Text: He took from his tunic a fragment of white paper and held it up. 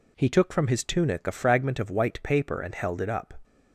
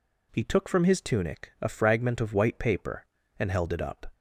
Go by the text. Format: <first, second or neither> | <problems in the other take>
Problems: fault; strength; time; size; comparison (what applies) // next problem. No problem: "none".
neither | none